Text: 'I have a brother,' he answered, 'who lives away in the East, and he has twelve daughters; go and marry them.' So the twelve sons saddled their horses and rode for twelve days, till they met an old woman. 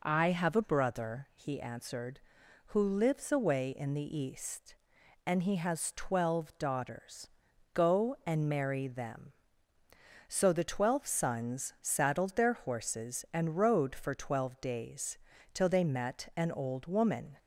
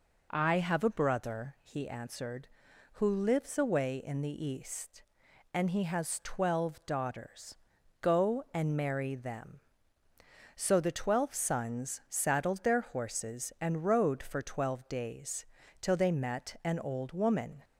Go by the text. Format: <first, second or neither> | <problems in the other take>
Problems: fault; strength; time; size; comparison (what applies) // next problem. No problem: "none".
neither | none